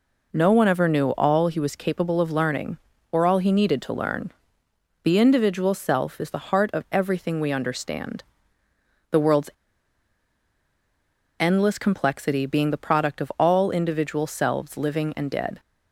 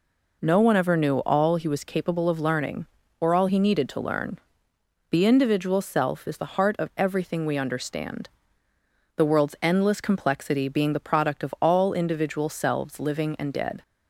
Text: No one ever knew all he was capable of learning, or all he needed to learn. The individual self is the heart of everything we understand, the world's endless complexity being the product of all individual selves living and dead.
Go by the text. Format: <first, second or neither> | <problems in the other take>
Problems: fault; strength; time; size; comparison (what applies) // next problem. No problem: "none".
second | pauses between "world's" and "endless"; strong; at 9.5 s; 1.8 s long